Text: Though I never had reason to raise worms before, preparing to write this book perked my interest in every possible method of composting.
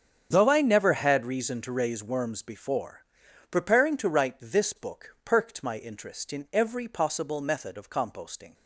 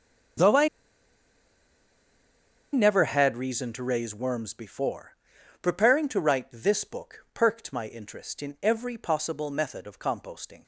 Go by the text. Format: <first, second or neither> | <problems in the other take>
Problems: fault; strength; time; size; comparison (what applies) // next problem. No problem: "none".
first | starts louder than the rest; strong; until 3.4 s; 7.5 dB; strong in the first // pauses between "I" and "never"; strong; at 0.6 s; 2.0 s long